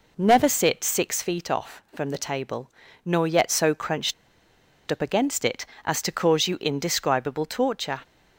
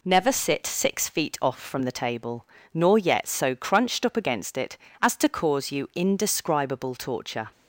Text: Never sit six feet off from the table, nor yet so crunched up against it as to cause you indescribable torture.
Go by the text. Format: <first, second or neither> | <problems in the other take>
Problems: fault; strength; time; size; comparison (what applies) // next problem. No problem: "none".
second | pauses between "crunched" and "up"; noticeable; at 4.1 s; 0.76 s long